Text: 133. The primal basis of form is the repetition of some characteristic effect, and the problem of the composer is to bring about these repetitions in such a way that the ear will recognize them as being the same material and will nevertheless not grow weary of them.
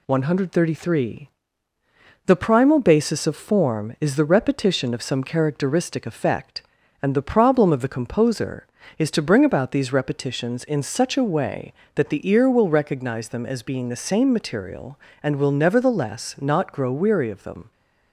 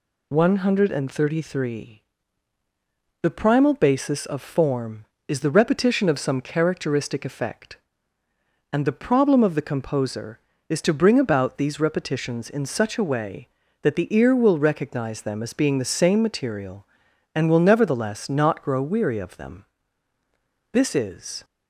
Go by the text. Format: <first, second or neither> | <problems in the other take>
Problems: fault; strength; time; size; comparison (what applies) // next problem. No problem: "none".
first | goes on to say "This is"; noticeable; from 20.7 s on; 0.72 s long